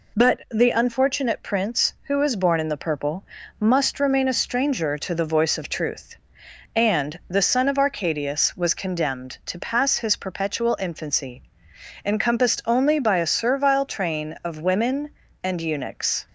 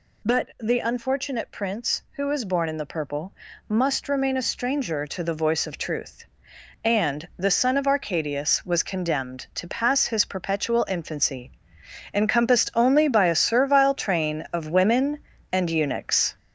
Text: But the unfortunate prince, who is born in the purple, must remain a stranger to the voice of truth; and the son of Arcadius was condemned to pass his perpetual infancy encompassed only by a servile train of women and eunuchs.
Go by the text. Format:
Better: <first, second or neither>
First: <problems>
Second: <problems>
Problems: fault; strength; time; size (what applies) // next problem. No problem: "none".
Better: first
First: pauses between "infancy" and "encompassed"; noticeable; at 11.4 s; 0.62 s long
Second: gets louder; noticeable; throughout; 6 dB // pauses between "infancy" and "encompassed"; noticeable; at 11.5 s; 0.62 s long